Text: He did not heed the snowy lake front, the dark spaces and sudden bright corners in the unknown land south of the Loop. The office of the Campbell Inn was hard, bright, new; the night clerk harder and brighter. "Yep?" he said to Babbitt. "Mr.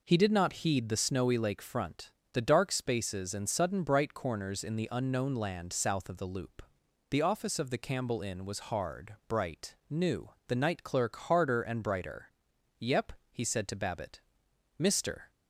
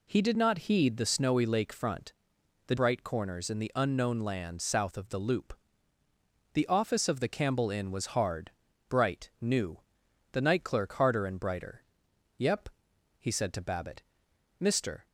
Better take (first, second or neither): first